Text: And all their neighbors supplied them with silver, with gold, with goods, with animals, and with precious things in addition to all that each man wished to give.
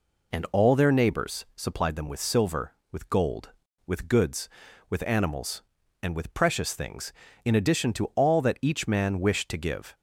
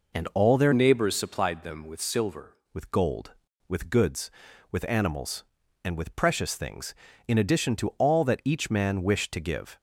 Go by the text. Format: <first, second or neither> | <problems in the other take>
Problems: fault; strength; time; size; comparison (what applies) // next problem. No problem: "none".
first | changes voice from "neighbors" to "silver"; from 0.7 to 2.5 s; 1.8 s long